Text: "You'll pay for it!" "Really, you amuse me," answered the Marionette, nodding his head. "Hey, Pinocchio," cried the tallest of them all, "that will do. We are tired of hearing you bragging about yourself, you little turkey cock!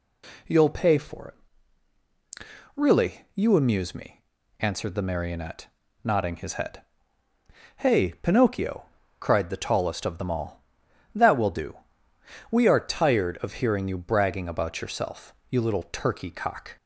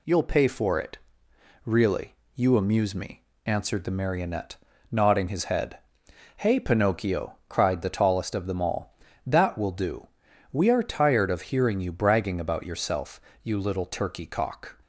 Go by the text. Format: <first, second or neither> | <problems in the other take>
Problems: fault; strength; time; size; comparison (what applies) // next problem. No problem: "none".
neither | none